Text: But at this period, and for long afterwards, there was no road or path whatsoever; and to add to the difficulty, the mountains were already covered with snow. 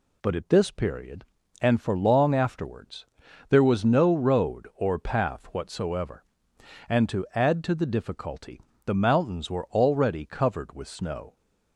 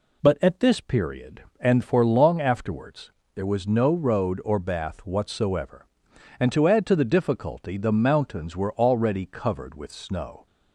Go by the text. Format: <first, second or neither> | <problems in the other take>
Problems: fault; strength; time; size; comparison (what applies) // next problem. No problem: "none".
first | says "bath" for "path"; at 4.5 s